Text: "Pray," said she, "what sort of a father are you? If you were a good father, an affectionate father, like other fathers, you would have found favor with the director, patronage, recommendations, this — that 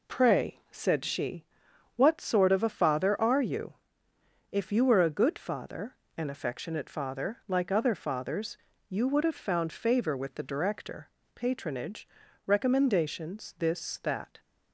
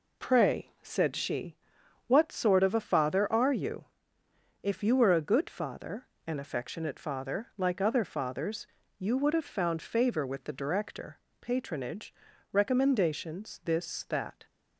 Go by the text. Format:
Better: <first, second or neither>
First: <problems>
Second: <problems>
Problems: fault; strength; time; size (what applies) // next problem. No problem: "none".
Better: neither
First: none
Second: none